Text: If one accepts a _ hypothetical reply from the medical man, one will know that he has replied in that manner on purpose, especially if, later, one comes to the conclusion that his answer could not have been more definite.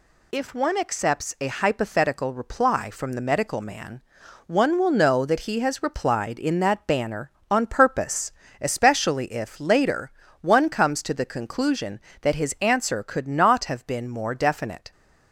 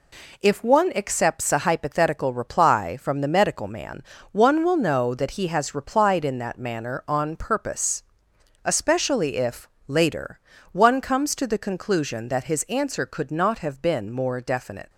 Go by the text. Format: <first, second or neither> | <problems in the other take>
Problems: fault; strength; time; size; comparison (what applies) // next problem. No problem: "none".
second | says "banner" for "manner"; at 6.8 s